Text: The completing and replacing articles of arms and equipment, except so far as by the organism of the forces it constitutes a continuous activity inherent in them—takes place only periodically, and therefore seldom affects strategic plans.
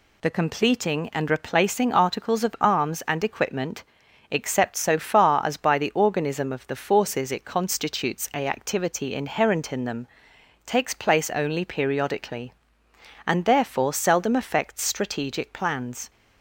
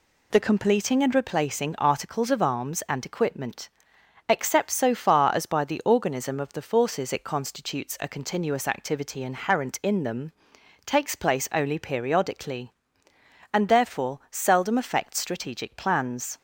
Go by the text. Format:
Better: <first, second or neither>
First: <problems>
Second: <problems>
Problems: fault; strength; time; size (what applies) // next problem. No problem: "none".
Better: second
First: skips "continuous"; at 8.4 s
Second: none